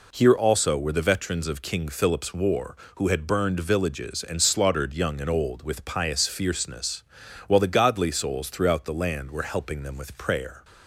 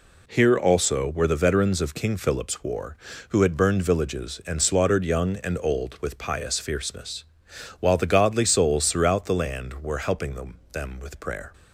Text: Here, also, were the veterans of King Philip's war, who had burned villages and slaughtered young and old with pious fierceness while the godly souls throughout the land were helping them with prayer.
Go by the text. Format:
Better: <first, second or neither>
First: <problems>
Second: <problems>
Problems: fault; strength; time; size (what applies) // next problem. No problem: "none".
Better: first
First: pauses between "fierceness" and "while"; noticeable; at 7.0 s; 0.46 s long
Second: pauses between "fierceness" and "while"; noticeable; at 7.2 s; 0.54 s long // says "them" twice; at 10.7 s